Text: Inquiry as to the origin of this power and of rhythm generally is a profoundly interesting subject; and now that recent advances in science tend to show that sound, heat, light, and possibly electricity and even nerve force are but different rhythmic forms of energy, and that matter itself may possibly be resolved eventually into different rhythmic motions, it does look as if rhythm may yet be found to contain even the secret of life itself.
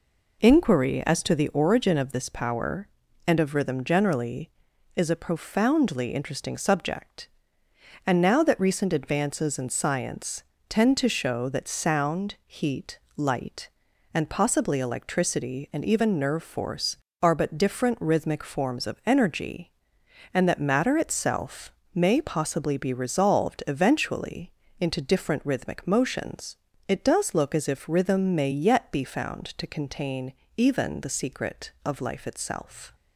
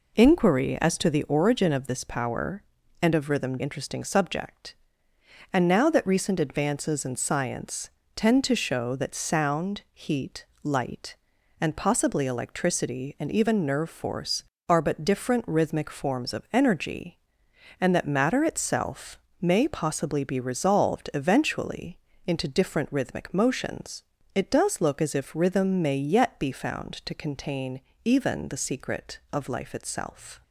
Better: first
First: pauses between "science" and "tend"; slight; at 10.4 s; 0.24 s long // pauses between "itself" and "may"; slight; at 21.7 s; 0.22 s long // pauses between "eventually" and "into"; slight; at 24.5 s; 0.30 s long // pauses between "contain" and "even"; slight; at 30.3 s; 0.22 s long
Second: skips "generally is a profoundly"; at 3.5 s // pauses between "science" and "tend"; slight; at 7.9 s; 0.24 s long // pauses between "itself" and "may"; slight; at 19.1 s; 0.22 s long // pauses between "eventually" and "into"; slight; at 21.9 s; 0.30 s long // pauses between "contain" and "even"; slight; at 27.8 s; 0.22 s long

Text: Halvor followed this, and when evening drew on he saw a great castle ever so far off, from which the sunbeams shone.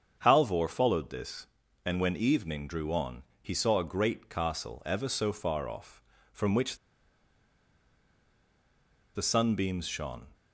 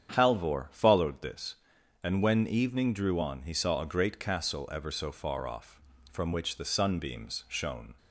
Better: second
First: starts louder than the rest; strong; until 1.2 s; 7.5 dB // pauses between "on" and "he"; slight; at 3.2 s; 0.20 s long // pauses between "which" and "the"; strong; at 6.7 s; 2.3 s long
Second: starts louder than the rest; strong; until 1.1 s; 8.5 dB

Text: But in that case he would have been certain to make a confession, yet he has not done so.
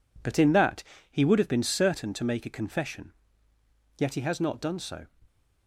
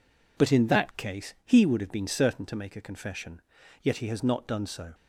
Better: second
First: skips "case"; at 0.9 s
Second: none

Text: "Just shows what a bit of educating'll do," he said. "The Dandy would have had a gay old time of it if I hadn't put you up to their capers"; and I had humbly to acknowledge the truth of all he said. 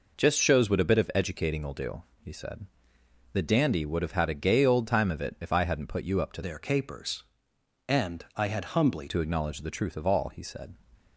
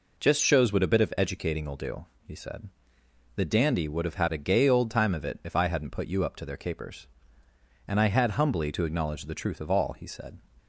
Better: second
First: changes voice from "their" to "humbly"; from 6.4 to 9.0 s; 2.6 s long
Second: none

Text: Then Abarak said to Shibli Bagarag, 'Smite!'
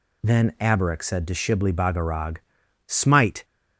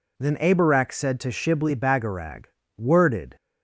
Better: first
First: none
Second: says "Worded" for "Smite"; at 2.7 s

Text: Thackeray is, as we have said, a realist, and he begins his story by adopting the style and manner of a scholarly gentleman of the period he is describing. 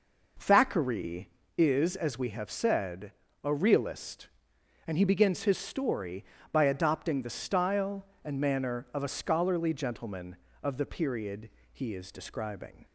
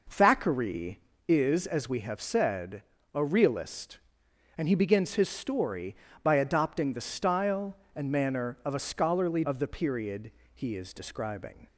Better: first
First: pauses between "period" and "he"; slight; at 11.4 s; 0.24 s long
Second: skips "gentleman"; at 9.4 s // pauses between "period" and "he"; slight; at 10.3 s; 0.24 s long

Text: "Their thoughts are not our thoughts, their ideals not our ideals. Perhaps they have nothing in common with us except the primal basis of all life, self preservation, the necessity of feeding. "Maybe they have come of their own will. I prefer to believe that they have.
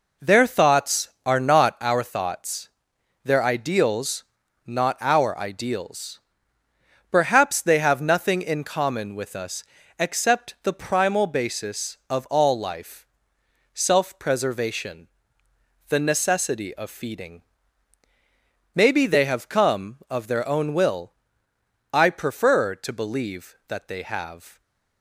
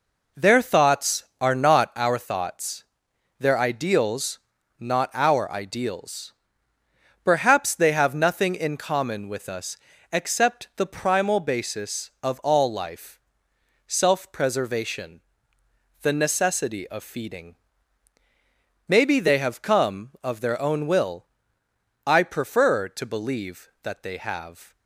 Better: neither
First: pauses between "ideals" and "not"; noticeable; at 4.2 s; 0.46 s long // pauses between "us" and "except"; slight; at 9.6 s; 0.34 s long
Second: pauses between "ideals" and "not"; at 4.3 s; 0.44 s long // pauses between "us" and "except"; slight; at 9.7 s; 0.34 s long

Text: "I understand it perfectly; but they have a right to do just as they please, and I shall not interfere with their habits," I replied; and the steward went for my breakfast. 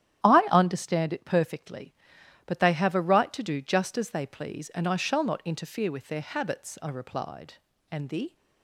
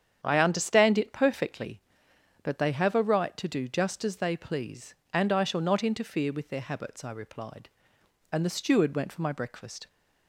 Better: second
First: starts louder than the rest; strong; until 1.3 s; 11.5 dB // stops before "steward went for my breakfast"; at 8.3 s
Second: starts louder than the rest; strong; until 1.2 s; 8.5 dB

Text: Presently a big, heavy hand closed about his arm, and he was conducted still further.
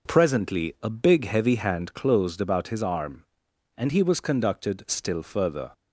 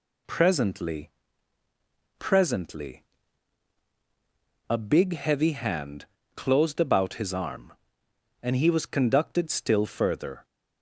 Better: first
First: none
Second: says "Presently" twice; at 2.1 s // pauses between "hand" and "closed"; slight; at 6.0 s; 0.32 s long

